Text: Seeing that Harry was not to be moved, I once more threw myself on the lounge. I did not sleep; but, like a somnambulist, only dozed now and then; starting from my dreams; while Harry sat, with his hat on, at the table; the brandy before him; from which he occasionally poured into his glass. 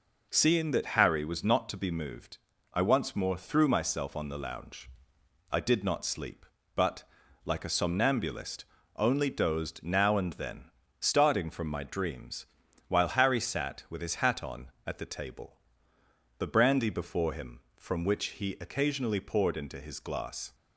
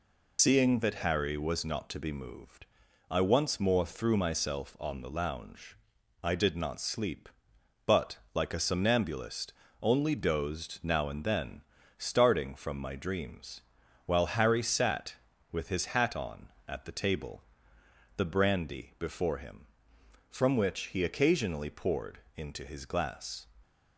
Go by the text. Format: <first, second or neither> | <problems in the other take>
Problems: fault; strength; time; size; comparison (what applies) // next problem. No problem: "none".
first | loses the start of "Seeing"; at 0.3 s; 110 ms // pauses between "poured" and "into"; slight; at 22.1 s; 0.16 s long